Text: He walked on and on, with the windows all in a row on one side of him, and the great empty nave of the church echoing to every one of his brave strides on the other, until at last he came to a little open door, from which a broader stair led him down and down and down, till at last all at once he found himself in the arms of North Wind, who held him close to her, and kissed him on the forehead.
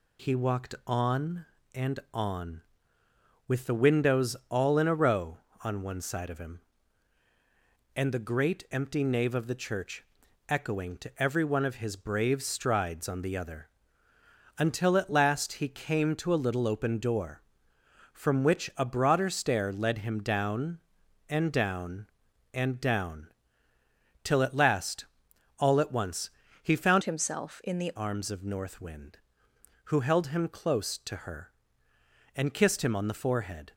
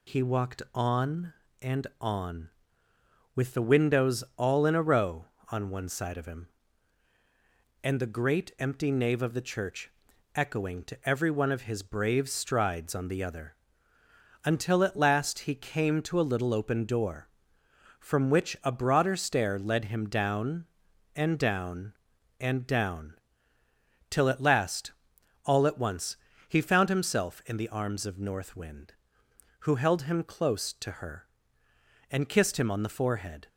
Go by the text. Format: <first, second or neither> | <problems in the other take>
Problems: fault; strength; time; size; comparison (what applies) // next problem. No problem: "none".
second | pauses between "church" and "echoing"; at 10.0 s; 0.42 s long; also in the second // pauses between "last" and "all"; noticeable; at 25.0 s; 0.52 s long; noticeable in the second // pauses between "once" and "he"; slight; at 26.2 s; 0.34 s long; slight in the second // changes voice from "himself" to "the"; from 27.0 to 27.9 s; 0.9 s long